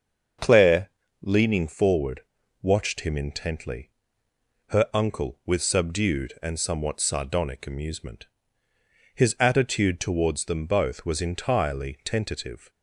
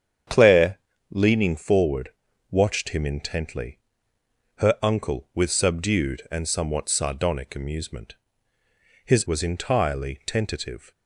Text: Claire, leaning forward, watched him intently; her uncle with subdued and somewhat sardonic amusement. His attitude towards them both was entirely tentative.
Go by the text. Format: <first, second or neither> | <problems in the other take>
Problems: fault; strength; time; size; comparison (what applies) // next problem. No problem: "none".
first | starts louder than the rest; strong; until 1.6 s; 8 dB; also in the first // skips "attitude towards them both"; at 9.2 s